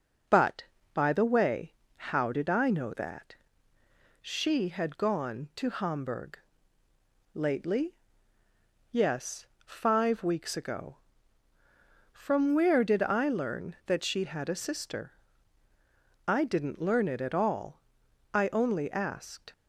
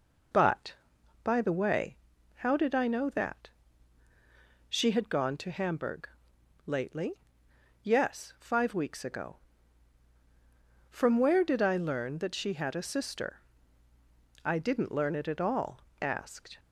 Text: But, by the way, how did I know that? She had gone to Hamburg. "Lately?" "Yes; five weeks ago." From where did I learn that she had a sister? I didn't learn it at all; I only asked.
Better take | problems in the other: first | skips "I only"; at 15.9 s

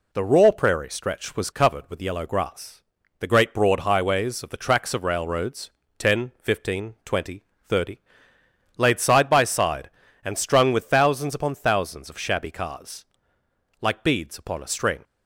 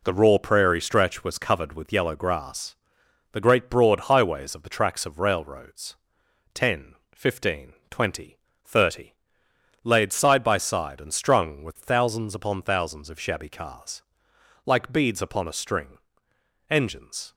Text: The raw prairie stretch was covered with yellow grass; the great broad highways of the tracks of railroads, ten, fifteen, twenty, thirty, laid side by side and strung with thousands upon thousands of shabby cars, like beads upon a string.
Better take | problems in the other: first | goes on to say "Engines"; noticeable; from 16.6 s on; 0.64 s long

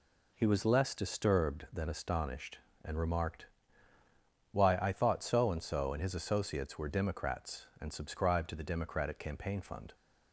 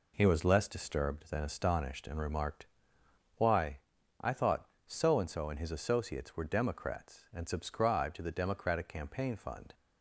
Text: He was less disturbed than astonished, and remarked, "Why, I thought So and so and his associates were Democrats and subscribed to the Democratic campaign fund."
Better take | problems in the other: neither | none

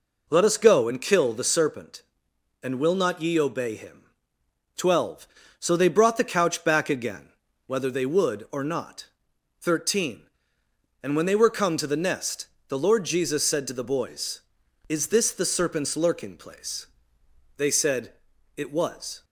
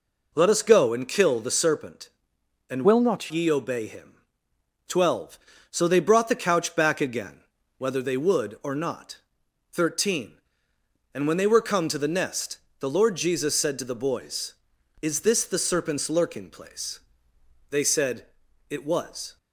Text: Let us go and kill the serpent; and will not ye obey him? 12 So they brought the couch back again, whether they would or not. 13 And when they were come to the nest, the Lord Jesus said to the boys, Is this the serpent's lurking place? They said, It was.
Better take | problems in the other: first | changes voice from "will" to "not"; from 2.8 to 3.3 s; 0.5 s long

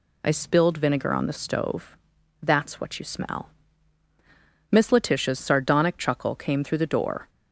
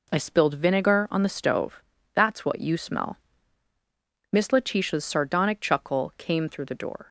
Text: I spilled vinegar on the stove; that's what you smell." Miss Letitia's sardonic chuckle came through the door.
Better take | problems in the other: neither | none

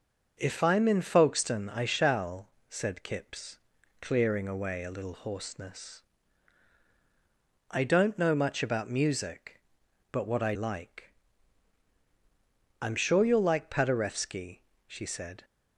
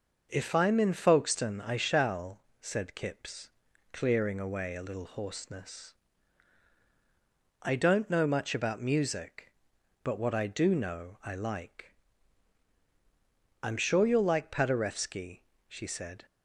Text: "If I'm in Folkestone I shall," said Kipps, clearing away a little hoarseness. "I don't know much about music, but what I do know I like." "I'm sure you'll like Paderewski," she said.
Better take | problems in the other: second | starts louder than the rest; noticeable; until 1.3 s; 6 dB // skips "do know I"; at 10.5 s

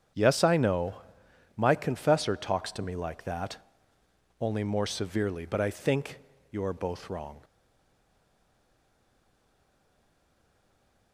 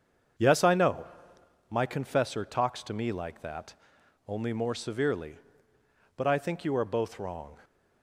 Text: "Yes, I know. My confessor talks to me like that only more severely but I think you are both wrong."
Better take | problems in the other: second | starts louder than the rest; strong; until 1.7 s; 8.5 dB; also in the second // pauses between "that" and "only"; noticeable; at 3.5 s; 0.86 s long; noticeable in the second // pauses between "think" and "you"; slight; at 6.1 s; 0.32 s long // stays silent after the last word; strong; from 7.4 s on; 3.7 s long

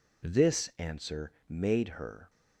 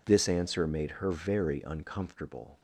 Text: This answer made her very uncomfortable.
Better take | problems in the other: second | pauses between "answer" and "made"; slight; at 1.3 s; 0.18 s long // stops before "very uncomfortable"; at 2.2 s

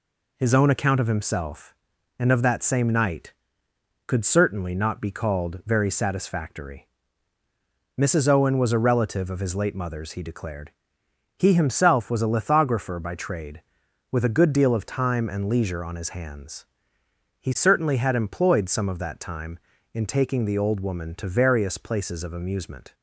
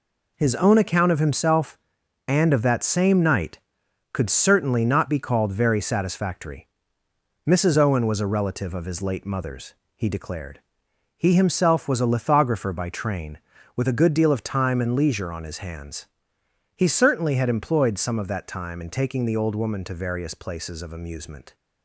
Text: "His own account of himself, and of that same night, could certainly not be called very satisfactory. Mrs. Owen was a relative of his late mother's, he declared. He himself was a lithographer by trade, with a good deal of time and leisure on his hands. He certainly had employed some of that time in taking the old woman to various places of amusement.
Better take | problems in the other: first | says "train" for "trade"; at 12.8 s

